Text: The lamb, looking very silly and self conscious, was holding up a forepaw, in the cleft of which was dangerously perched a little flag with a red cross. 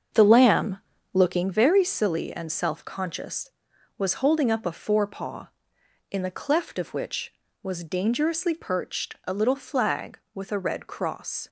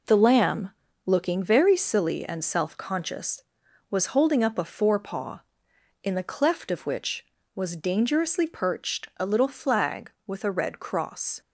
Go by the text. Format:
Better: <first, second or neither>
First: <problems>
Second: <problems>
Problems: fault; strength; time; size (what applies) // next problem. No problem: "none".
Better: second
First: starts louder than the rest; until 1.5 s; 6.5 dB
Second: none